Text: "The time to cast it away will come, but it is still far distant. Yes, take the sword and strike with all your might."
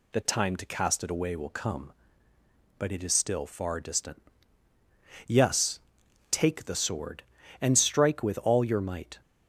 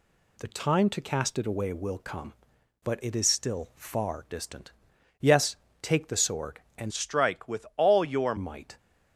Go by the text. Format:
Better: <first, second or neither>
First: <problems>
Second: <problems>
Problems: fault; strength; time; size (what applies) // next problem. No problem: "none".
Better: first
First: none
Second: changes voice from "strike" to "your"; from 6.9 to 8.3 s; 1.4 s long